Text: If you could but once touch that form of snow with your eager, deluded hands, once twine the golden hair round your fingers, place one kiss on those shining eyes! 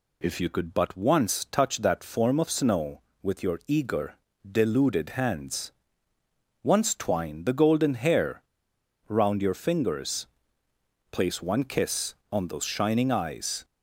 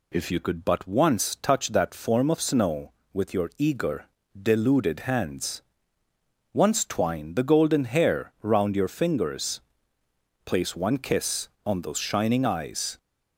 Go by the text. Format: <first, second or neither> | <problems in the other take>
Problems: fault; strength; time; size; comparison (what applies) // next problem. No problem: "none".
second | pauses between "hair" and "round"; noticeable; at 8.4 s; 0.66 s long